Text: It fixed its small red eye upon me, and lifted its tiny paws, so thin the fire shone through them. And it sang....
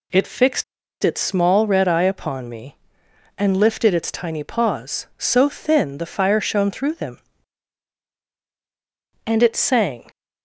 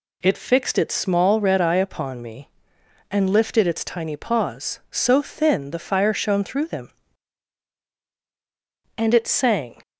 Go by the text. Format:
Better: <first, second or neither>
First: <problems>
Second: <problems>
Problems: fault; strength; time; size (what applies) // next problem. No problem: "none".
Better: second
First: pauses between "fixed" and "its"; at 0.6 s; 0.39 s long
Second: none